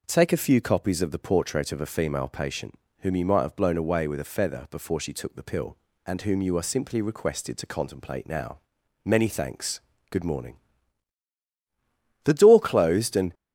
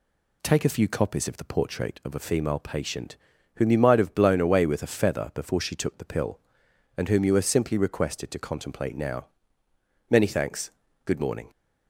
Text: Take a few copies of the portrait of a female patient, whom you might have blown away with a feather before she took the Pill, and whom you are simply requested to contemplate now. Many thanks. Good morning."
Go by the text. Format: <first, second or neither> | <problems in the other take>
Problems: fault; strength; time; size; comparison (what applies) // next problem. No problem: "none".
second | goes on to say "The door closed and"; noticeable; from 12.2 s on; 1.0 s long